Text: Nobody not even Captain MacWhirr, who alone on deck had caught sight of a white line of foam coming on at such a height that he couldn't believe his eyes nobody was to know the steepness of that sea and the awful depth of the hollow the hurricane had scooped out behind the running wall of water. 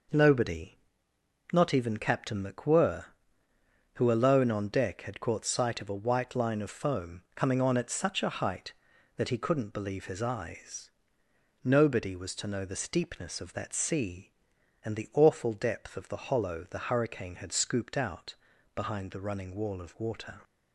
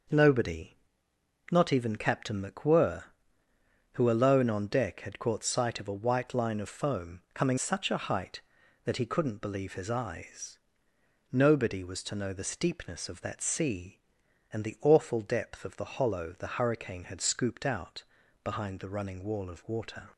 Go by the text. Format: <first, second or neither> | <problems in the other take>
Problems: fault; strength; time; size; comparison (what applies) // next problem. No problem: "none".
first | pauses between "Nobody" and "not"; noticeable; at 0.7 s; 0.76 s long; noticeable in the first // skips "on at"; at 7.5 s // pauses between "eyes" and "nobody"; noticeable; at 10.5 s; 0.74 s long; noticeable in the first // pauses between "out" and "behind"; at 18.0 s; 0.40 s long; also in the first